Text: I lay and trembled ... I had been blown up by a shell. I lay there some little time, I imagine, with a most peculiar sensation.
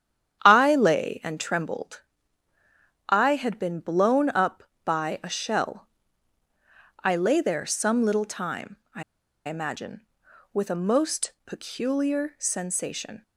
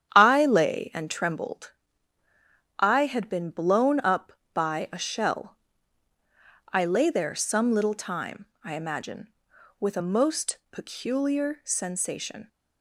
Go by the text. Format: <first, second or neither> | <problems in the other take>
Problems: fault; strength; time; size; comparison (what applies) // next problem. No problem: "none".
second | starts louder than the rest; strong; until 1.4 s; 9.5 dB; strong in the second // pauses between "I" and "imagine"; at 9.0 s; 0.45 s long